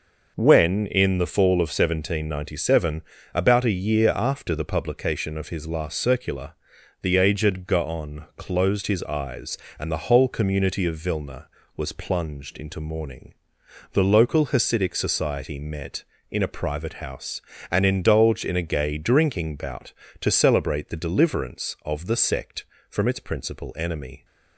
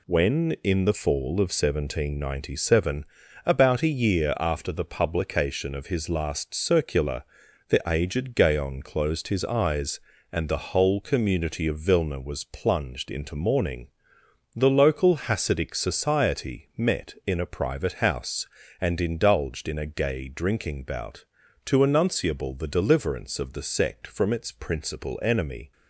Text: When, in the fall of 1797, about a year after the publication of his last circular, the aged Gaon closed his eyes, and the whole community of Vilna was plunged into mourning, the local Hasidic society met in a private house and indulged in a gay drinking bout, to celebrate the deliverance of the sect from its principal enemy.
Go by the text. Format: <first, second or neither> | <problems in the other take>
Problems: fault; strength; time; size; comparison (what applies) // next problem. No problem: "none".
first | says "enunciable" for "celebrate"; at 21.7 s